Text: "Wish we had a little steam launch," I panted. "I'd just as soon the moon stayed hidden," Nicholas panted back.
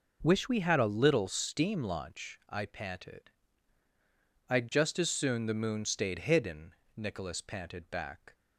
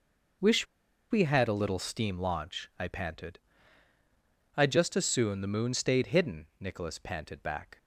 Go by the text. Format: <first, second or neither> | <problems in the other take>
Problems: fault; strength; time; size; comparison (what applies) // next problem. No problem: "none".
first | pauses between "Wish" and "we"; at 0.6 s; 0.45 s long